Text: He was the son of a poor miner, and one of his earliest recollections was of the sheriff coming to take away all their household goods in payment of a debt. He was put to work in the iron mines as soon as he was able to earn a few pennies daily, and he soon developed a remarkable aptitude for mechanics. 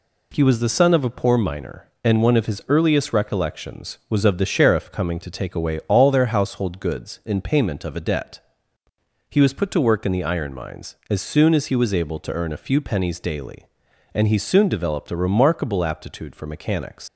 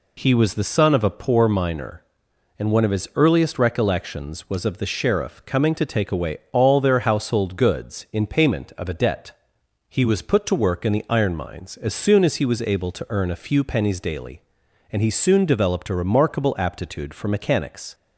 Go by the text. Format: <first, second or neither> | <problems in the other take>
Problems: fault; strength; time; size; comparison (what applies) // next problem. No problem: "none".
second | leaves "mechanics" unfinished; at 17.0 s; 85 ms